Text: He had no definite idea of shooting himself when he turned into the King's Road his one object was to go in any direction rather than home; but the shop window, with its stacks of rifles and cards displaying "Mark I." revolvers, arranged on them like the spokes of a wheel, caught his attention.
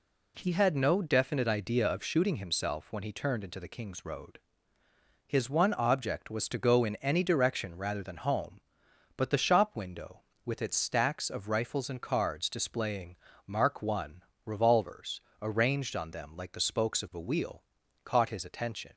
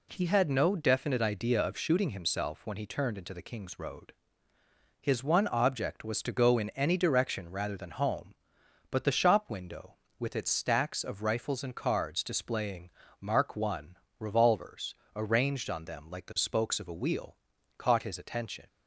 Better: neither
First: pauses between "Road" and "his"; noticeable; at 4.3 s; 0.88 s long // pauses between "displaying" and "Mark"; slight; at 13.1 s; 0.32 s long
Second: pauses between "Road" and "his"; noticeable; at 4.1 s; 0.88 s long // pauses between "displaying" and "Mark"; slight; at 12.8 s; 0.32 s long

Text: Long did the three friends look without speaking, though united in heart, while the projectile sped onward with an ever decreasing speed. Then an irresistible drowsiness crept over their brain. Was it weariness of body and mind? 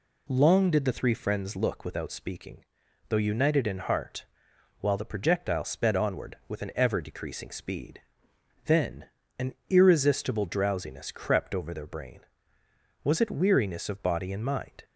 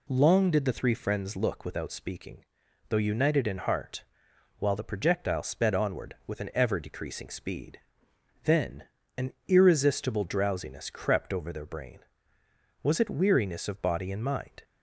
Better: neither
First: pauses between "Then" and "an"; slight; at 9.0 s; 0.32 s long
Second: pauses between "Then" and "an"; slight; at 8.8 s; 0.32 s long

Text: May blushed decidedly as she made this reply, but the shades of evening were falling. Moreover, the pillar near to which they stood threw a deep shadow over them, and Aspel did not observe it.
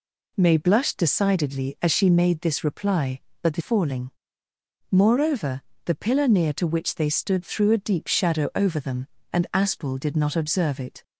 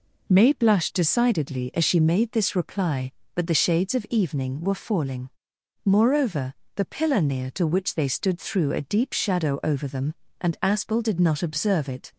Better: second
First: skips "shades of evening were"; at 3.6 s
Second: none

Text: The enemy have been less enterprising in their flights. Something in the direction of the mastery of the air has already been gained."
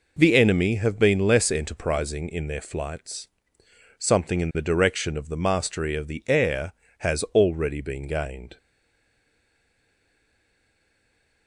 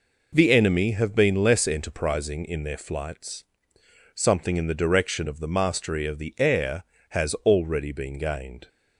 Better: second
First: stays silent after the last word; strong; from 8.5 s on; 2.9 s long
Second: none

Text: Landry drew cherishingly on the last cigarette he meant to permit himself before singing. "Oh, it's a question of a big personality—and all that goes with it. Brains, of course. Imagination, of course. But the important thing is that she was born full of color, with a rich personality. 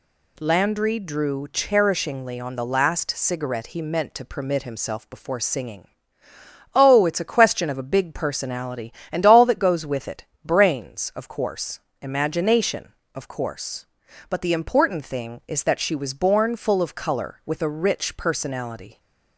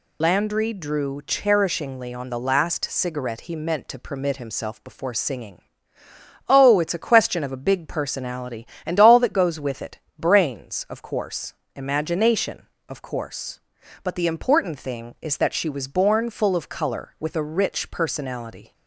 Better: first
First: none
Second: loses the start of "Landry"; at 0.2 s; 85 ms

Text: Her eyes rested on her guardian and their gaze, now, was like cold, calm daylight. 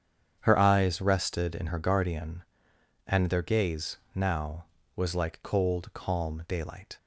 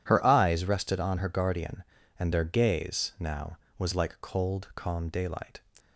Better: second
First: starts louder than the rest; strong; until 1.4 s; 8 dB // says "in" for "on"; at 1.5 s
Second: none

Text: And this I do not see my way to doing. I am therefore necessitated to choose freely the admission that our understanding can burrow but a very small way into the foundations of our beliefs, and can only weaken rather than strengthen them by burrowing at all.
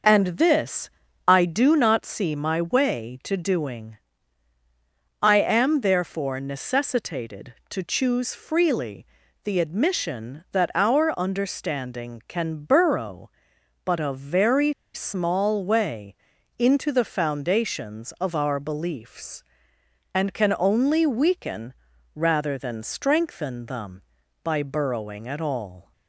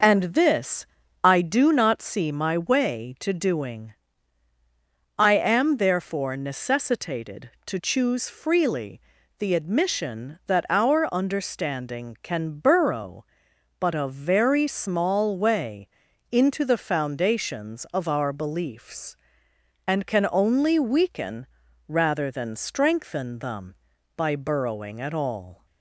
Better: second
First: starts louder than the rest; noticeable; until 1.4 s; 6 dB // pauses between "this" and "I"; slight; at 0.9 s; 0.36 s long // pauses between "freely" and "the"; slight; at 9.0 s; 0.36 s long // pauses between "very" and "small"; slight; at 14.7 s; 0.21 s long // pauses between "way" and "into"; at 16.1 s; 0.42 s long // pauses between "weaken" and "rather"; at 21.7 s; 0.40 s long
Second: pauses between "this" and "I"; slight; at 0.8 s; 0.36 s long // pauses between "freely" and "the"; slight; at 9.0 s; 0.36 s long // pauses between "way" and "into"; at 15.8 s; 0.42 s long // pauses between "weaken" and "rather"; at 21.4 s; 0.40 s long

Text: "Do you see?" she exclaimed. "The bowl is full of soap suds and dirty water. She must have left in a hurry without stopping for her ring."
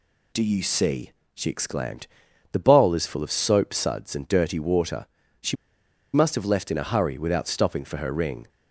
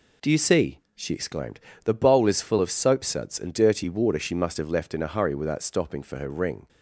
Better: second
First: pauses between "She" and "must"; noticeable; at 5.5 s; 0.60 s long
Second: none

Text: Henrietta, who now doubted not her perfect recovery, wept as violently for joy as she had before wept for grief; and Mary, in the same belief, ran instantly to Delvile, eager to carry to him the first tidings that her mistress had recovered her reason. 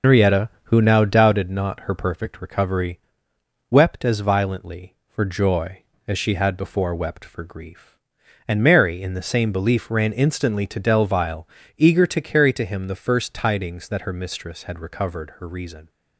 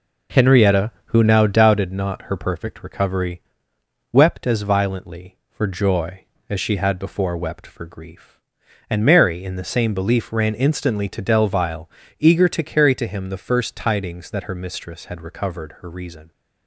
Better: second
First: loses the start of "Henrietta"; at 0.0 s; 160 ms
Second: none

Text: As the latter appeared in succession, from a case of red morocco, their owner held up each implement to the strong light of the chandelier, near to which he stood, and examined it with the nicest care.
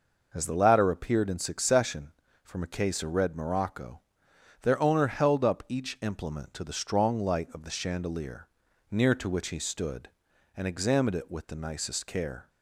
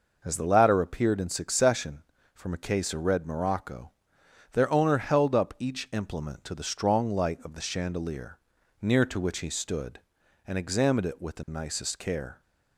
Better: neither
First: none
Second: none

